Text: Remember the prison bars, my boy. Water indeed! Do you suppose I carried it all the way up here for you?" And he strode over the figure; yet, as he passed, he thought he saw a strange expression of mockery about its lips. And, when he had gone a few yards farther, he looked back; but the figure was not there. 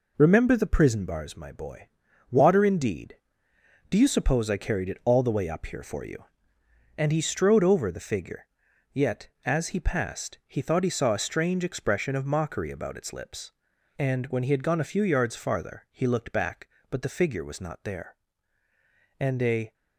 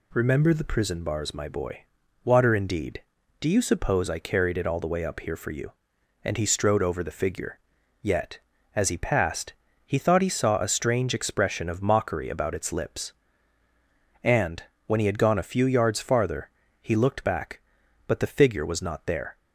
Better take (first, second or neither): second